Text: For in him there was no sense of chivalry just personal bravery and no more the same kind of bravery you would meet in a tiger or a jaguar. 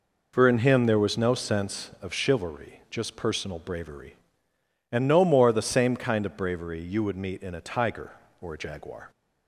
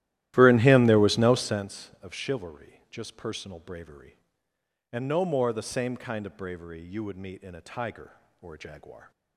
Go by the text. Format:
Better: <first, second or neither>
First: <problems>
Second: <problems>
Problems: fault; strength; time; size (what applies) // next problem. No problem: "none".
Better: first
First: none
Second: starts louder than the rest; strong; until 1.7 s; 14 dB